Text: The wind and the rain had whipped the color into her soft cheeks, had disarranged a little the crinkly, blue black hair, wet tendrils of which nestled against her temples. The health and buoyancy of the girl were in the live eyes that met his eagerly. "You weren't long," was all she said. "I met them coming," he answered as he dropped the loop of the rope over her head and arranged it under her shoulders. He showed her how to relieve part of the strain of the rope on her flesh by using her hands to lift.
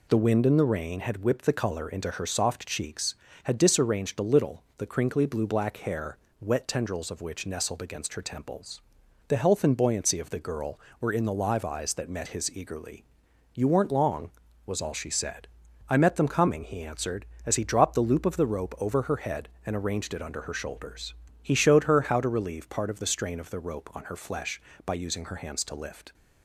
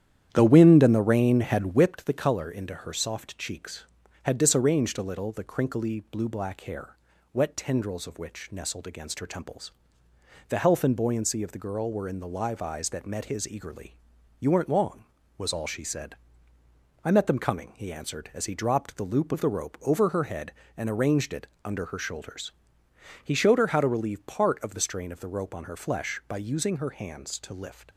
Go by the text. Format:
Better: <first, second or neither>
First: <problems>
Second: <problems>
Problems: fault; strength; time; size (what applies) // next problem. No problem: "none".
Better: first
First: none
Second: starts louder than the rest; strong; until 1.9 s; 10 dB // pauses between "it" and "under"; slight; at 21.4 s; 0.16 s long